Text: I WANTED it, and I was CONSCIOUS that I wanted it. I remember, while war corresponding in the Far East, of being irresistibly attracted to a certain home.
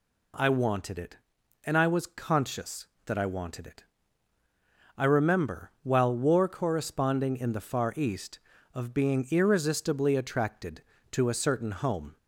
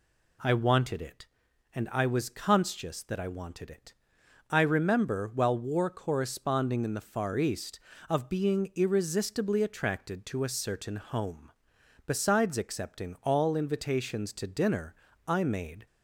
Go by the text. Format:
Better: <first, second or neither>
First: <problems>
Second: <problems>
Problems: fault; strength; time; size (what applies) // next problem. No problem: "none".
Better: first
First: none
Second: goes on to say "Besides accepting all invitations to dinner I made"; strong; from 12.0 s on; 3.8 s long